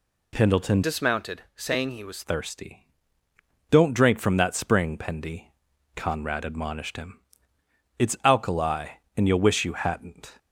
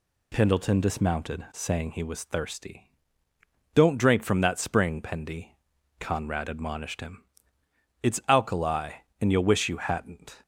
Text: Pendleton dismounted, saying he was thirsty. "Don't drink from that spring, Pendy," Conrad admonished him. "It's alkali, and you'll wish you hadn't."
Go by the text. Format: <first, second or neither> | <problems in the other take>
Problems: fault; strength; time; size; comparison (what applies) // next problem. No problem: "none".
second | changes voice from "dismounted" to "was"; from 0.8 to 2.2 s; 1.4 s long